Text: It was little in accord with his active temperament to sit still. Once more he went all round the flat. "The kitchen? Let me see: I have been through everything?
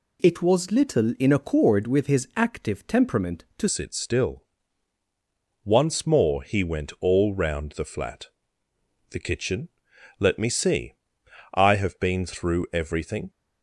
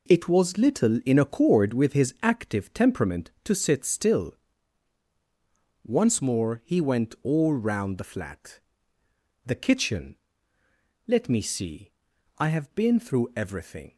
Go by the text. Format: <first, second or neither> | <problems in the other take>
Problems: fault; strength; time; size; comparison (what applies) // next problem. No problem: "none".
second | changes voice at "sit"; from 3.6 s on; 9.6 s long